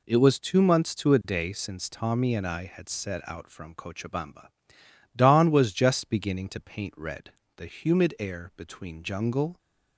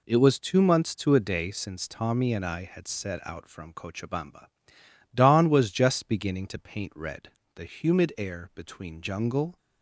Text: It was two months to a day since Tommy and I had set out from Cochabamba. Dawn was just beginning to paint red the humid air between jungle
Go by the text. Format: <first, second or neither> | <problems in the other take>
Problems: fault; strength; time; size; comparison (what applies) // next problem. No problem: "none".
neither | pauses between "red" and "the"; slight; the same in both